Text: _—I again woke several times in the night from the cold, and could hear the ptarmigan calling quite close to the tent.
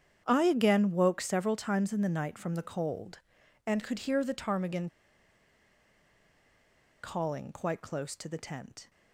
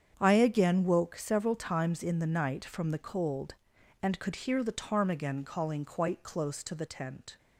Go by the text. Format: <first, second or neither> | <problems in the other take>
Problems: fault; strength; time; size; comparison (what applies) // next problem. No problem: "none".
second | starts louder than the rest; strong; until 1.2 s; 8.5 dB; strong in the second // pauses between "ptarmigan" and "calling"; strong; at 4.8 s; 2.1 s long